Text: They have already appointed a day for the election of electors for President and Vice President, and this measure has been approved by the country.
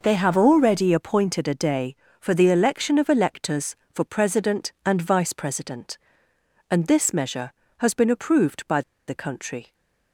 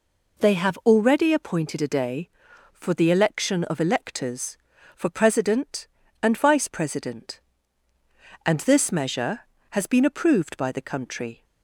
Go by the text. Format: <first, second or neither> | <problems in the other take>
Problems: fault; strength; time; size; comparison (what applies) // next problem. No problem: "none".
second | pauses between "by" and "the"; slight; at 8.8 s; 0.26 s long